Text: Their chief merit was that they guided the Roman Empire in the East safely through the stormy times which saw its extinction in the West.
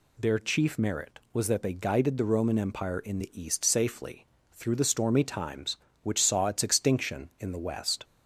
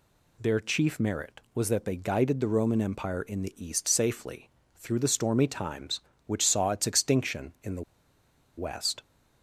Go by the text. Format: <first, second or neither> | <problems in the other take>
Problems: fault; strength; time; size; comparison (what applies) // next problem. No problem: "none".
first | pauses between "safely" and "through"; slight; at 4.4 s; 0.26 s long; slight in the first // pauses between "the" and "West"; noticeable; at 7.8 s; 0.75 s long